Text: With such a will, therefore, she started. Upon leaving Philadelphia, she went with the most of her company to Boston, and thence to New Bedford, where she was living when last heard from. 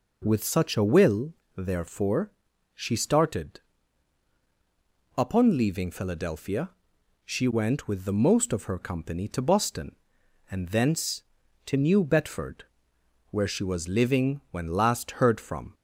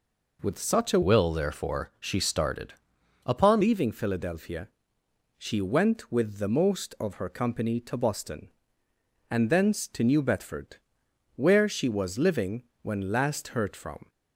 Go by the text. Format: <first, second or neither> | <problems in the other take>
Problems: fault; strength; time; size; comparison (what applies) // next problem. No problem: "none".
first | changes voice from "will" to "Upon"; from 1.0 to 3.6 s; 2.6 s long // pauses between "living" and "when"; slight; at 12.6 s; 0.18 s long